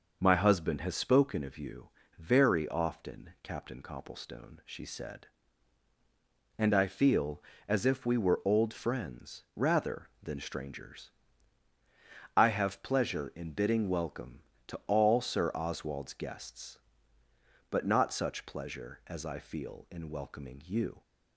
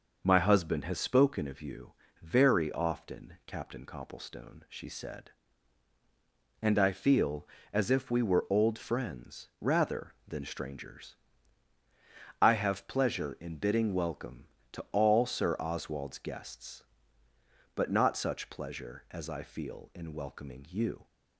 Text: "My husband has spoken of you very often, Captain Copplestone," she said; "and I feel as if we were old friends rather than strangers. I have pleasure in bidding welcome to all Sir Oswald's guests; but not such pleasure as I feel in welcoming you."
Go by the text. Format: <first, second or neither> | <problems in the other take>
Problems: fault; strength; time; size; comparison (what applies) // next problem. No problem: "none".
neither | pauses between "you" and "very"; slight; the same in both